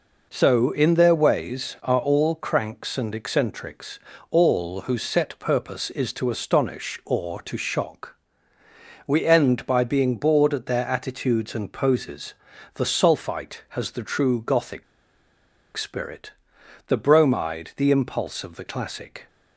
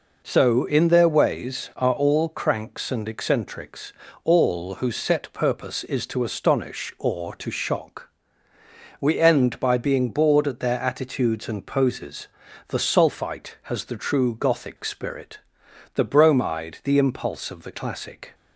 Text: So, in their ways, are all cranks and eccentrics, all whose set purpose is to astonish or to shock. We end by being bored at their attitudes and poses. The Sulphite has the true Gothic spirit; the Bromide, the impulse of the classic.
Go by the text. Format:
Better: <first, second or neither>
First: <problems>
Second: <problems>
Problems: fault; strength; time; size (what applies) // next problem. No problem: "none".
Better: second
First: pauses between "Gothic" and "spirit"; noticeable; at 14.8 s; 0.92 s long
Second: none